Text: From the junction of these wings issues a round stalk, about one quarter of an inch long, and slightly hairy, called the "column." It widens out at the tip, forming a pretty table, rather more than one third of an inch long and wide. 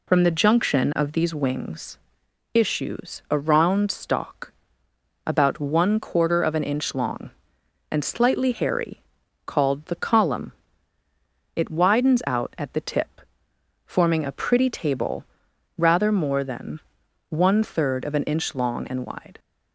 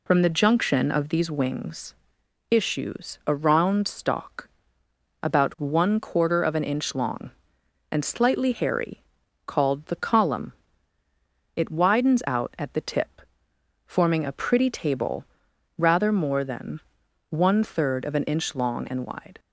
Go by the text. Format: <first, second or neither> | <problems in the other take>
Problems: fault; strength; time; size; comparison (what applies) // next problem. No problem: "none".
neither | pauses between "wings" and "issues"; noticeable; the same in both // pauses between "than" and "one"; noticeable; the same in both